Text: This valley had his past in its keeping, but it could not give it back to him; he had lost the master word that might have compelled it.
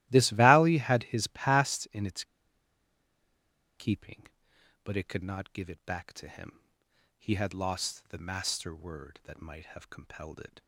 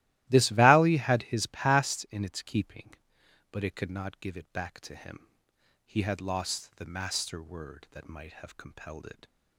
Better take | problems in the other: second | starts louder than the rest; strong; until 1.1 s; 16 dB; strong in the second // pauses between "its" and "keeping"; strong; at 2.2 s; 1.5 s long

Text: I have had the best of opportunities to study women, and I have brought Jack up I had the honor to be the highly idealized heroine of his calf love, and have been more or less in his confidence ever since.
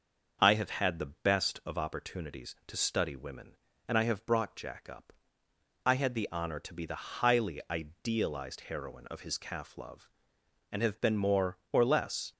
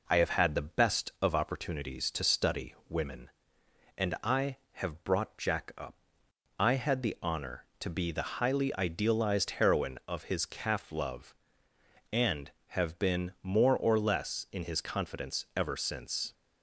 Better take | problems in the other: second | pauses between "up" and "I"; noticeable; at 5.1 s; 0.74 s long; noticeable in the second // stops before "in his confidence ever since"; at 12.3 s

